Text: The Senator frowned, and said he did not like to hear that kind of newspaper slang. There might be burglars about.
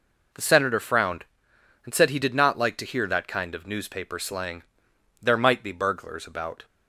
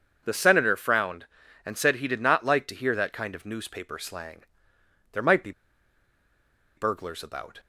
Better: first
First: none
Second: pauses between "be" and "burglars"; strong; at 5.5 s; 1.2 s long

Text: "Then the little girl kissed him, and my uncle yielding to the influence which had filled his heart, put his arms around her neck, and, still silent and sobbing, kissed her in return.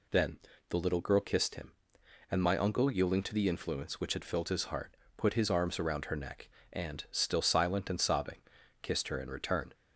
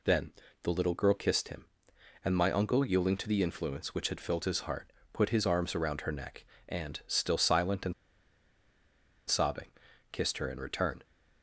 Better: first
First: pauses between "Then" and "the"; slight; at 0.3 s; 0.32 s long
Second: pauses between "Then" and "the"; slight; at 0.3 s; 0.32 s long // pauses between "and" and "sobbing"; strong; at 7.9 s; 1.3 s long

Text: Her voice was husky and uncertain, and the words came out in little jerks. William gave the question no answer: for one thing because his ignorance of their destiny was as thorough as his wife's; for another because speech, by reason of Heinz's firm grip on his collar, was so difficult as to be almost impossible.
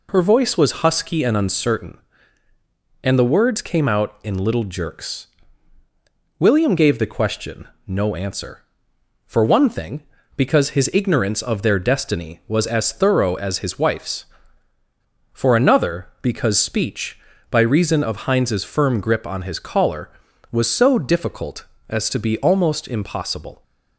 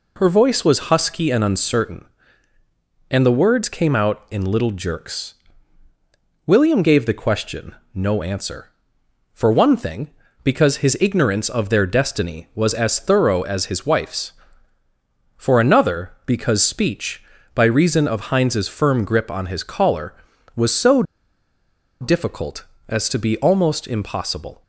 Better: first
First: pauses between "question" and "no"; slight; at 7.6 s; 0.18 s long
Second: pauses between "question" and "no"; slight; at 7.7 s; 0.18 s long // pauses between "so" and "difficult"; noticeable; at 21.0 s; 0.97 s long

